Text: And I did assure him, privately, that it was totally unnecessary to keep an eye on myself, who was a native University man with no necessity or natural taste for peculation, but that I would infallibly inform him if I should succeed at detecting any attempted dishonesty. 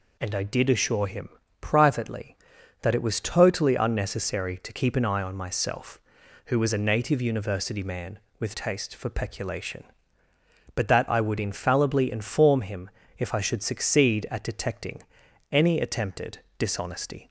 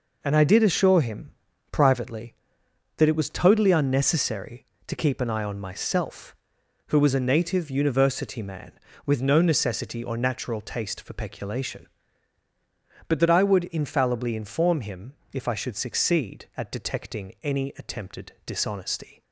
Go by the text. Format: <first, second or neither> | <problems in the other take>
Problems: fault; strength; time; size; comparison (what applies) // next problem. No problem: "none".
second | skips "no necessity or natural"; at 8.5 s // pauses between "him" and "if"; slight; at 12.8 s; 0.28 s long; slight in the second // pauses between "detecting" and "any"; noticeable; at 15.0 s; 0.50 s long // pauses between "attempted" and "dishonesty"; slight; at 16.3 s; 0.20 s long